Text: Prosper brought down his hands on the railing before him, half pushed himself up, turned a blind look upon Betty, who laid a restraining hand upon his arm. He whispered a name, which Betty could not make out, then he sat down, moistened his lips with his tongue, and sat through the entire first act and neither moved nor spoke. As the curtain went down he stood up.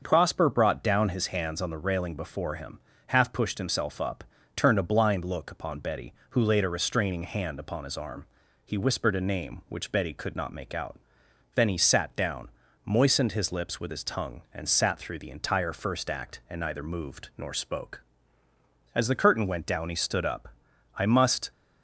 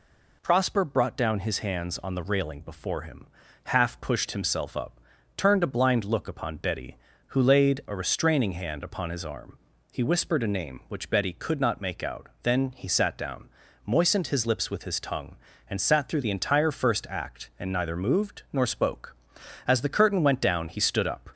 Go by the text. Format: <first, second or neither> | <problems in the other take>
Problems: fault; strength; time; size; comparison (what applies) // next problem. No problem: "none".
second | starts louder than the rest; until 1.0 s; 6.5 dB // goes on to say "I must"; from 20.9 s on; 0.54 s long